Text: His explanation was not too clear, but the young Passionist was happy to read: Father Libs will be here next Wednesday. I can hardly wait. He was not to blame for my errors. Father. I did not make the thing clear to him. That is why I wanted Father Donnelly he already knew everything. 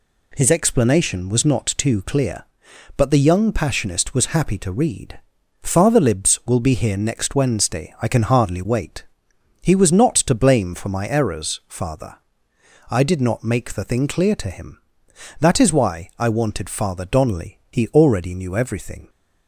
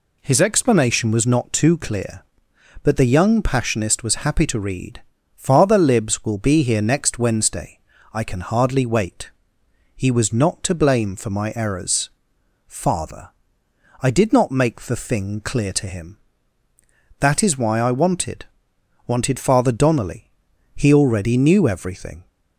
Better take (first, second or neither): first